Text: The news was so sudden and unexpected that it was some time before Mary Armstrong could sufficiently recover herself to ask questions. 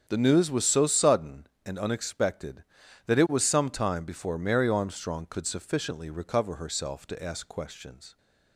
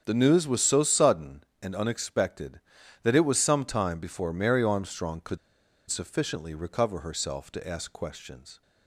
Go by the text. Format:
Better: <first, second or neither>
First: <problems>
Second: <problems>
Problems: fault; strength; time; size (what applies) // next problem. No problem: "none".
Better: first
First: starts louder than the rest; strong; until 1.0 s; 7.5 dB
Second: starts louder than the rest; strong; until 1.0 s; 8 dB // pauses between "could" and "sufficiently"; noticeable; at 5.3 s; 0.51 s long